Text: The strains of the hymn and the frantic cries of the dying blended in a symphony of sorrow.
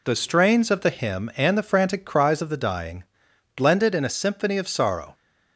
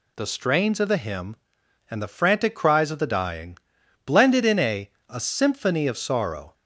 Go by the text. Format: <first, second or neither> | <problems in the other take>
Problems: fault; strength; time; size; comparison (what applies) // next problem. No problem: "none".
first | pauses between "dying" and "blended"; noticeable; at 3.5 s; 0.48 s long; noticeable in the first // says "a" twice; at 5.0 s